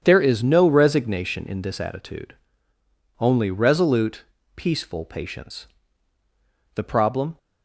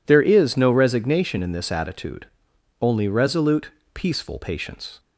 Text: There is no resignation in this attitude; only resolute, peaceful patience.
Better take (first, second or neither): second